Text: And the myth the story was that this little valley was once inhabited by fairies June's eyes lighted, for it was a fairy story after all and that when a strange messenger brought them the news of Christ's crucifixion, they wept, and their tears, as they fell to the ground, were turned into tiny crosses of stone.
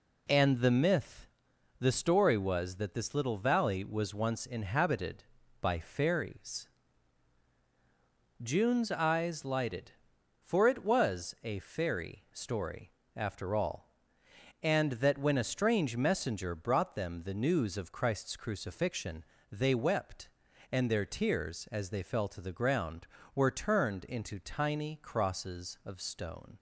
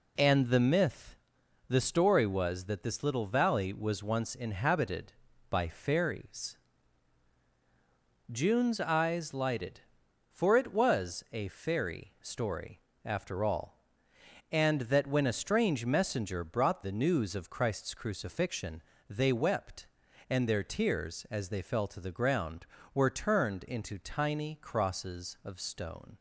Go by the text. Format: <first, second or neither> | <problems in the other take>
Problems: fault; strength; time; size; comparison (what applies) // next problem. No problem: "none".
first | pauses between "myth" and "the"; noticeable; at 1.1 s; 0.52 s long; noticeable in the first // pauses between "fairies" and "June's"; strong; at 6.5 s; 1.7 s long; strong in the first // pauses between "story" and "after"; slight; at 12.7 s; 0.26 s long; slight in the first // skips "them"; at 16.8 s